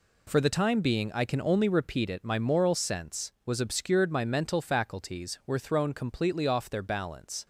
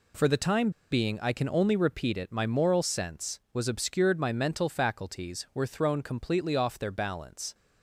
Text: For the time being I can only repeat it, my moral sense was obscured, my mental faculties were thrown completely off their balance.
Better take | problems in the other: first | pauses between "time" and "being"; slight; at 0.6 s; 0.21 s long

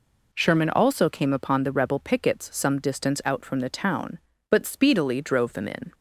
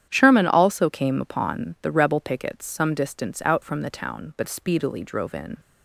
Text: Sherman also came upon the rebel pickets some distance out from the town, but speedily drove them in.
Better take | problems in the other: first | starts louder than the rest; strong; until 1.1 s; 10 dB // skips "them"; at 5.3 s

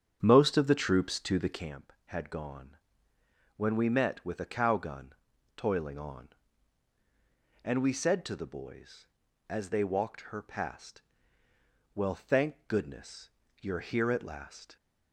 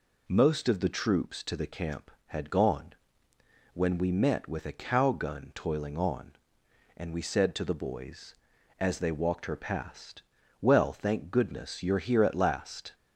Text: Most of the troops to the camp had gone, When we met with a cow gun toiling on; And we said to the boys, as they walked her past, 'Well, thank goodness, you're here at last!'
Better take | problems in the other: second | starts louder than the rest; strong; until 1.8 s; 8.5 dB // pauses between "gun" and "toiling"; at 5.1 s; 0.42 s long

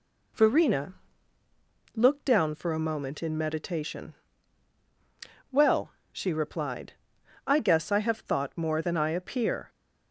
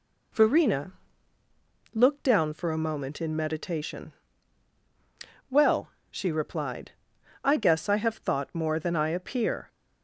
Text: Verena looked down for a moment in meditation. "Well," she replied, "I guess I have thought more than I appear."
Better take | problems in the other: neither | pauses between "Verena" and "looked"; the same in both

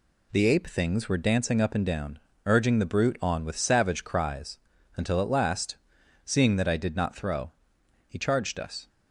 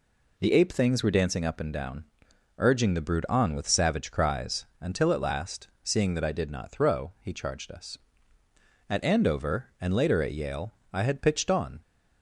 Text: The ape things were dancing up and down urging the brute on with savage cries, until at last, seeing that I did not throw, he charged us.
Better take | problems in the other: first | pauses between "down" and "urging"; noticeable; at 2.0 s; 0.54 s long; slight in the first // goes on to say "At Andover and later at Yale I had pitched on"; strong; from 8.8 s on; 2.9 s long

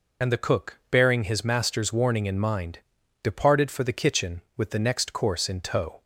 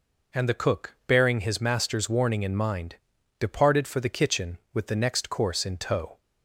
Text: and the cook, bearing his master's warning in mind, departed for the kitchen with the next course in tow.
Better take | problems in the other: second | loses the start of "and"; at 0.2 s; 35 ms

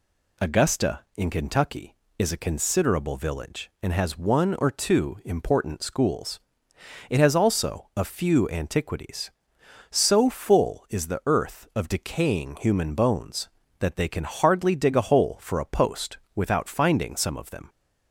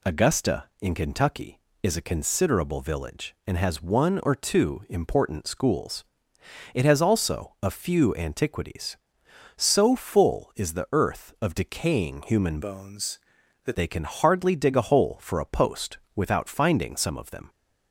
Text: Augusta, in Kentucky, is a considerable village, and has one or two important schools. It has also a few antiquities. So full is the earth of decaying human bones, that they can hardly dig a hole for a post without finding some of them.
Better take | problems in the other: first | changes voice from "bones" to "that"; from 12.6 to 13.7 s; 1.1 s long // pauses between "post" and "without"; slight; at 15.9 s; 0.18 s long; slight in the first

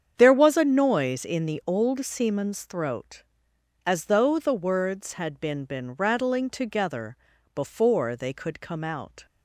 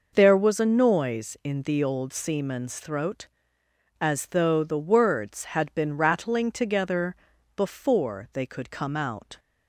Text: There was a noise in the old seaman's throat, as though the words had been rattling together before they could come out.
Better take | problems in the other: second | starts louder than the rest; strong; until 1.1 s; 8 dB // says "been" twice; at 5.6 s // pauses between "together" and "before"; at 7.1 s; 0.40 s long; also in the second

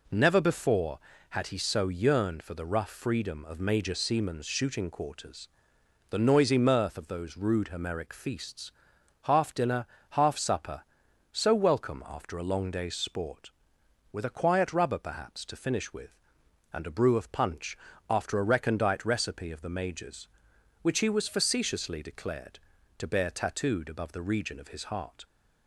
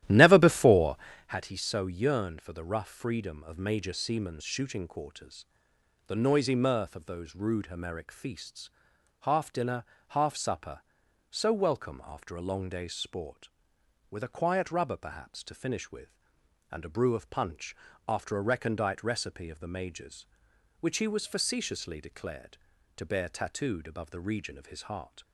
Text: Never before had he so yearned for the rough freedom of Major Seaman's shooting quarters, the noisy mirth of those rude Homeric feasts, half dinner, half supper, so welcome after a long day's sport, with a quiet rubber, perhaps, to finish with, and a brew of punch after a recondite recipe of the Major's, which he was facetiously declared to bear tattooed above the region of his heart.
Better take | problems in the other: first | starts louder than the rest; strong; until 1.4 s; 13 dB // pauses between "punch" and "after"; slight; at 17.7 s; 0.32 s long; slight in the first

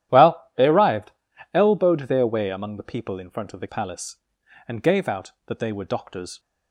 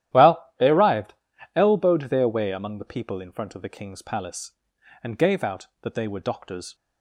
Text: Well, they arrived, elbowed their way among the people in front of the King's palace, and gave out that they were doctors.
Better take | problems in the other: second | starts louder than the rest; strong; until 1.6 s; 11.5 dB; strong in the second // skips "King's"; at 3.6 s

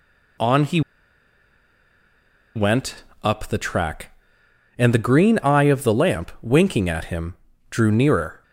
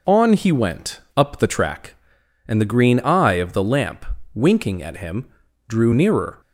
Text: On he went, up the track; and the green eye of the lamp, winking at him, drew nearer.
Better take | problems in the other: second | pauses between "he" and "went"; strong; at 0.7 s; 1.7 s long

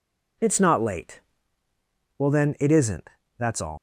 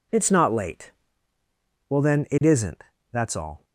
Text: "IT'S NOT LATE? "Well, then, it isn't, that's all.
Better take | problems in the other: second | leaves "all" unfinished; at 3.7 s; 110 ms

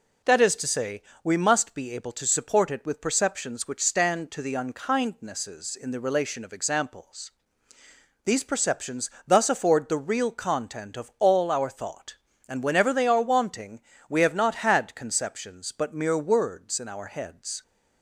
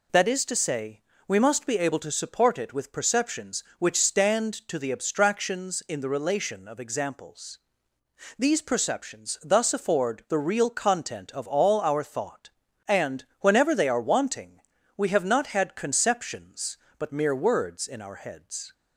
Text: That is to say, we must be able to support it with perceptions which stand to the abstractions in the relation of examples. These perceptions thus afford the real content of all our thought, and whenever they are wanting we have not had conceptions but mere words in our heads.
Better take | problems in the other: second | says "unkindnesses" for "abstractions"; at 4.5 s // pauses between "perceptions" and "thus"; slight; at 9.1 s; 0.16 s long // pauses between "wanting" and "we"; slight; at 13.8 s; 0.28 s long; also in the second

